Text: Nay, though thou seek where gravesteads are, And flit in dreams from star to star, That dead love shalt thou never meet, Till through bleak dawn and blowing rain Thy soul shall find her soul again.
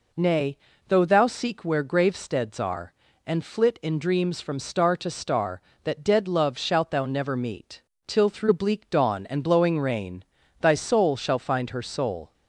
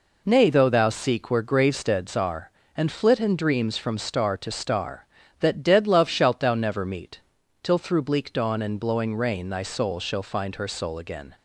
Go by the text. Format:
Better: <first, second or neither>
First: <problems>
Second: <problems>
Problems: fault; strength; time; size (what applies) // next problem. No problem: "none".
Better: second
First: pauses between "rain" and "Thy"; at 10.2 s; 0.38 s long // stops before "again"; at 12.3 s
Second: none